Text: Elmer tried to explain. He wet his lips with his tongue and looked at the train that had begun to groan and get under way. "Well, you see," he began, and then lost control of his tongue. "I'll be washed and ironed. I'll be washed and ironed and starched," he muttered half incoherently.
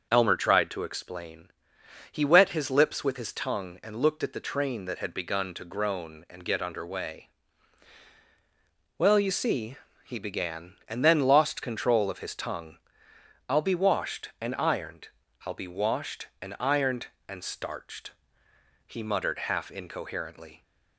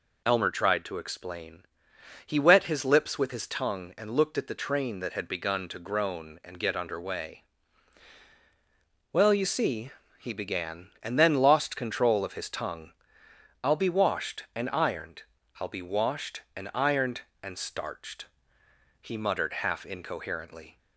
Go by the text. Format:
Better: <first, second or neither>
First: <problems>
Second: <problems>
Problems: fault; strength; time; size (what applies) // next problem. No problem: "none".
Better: second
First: starts louder than the rest; until 1.0 s; 6.5 dB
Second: none